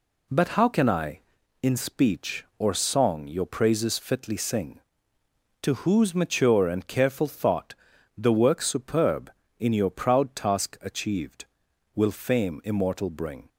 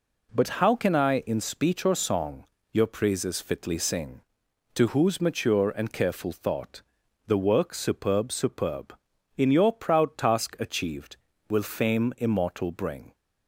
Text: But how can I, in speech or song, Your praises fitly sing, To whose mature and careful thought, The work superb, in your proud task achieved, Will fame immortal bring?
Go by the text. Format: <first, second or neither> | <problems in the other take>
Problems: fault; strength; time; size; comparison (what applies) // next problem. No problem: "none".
first | says "superb" twice; at 8.3 s